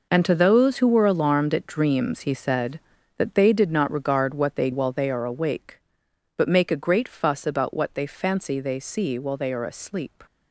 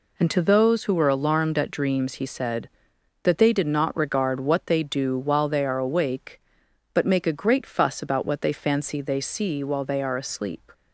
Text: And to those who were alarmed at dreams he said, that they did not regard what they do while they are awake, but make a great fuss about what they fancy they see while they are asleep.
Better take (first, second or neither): second